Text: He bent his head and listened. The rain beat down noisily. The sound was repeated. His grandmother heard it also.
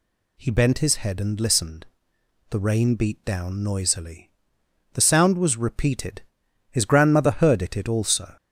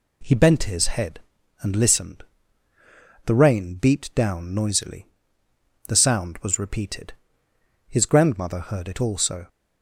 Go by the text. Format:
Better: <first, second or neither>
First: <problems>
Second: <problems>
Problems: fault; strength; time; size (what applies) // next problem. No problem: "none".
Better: second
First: says "it" twice; at 7.7 s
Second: none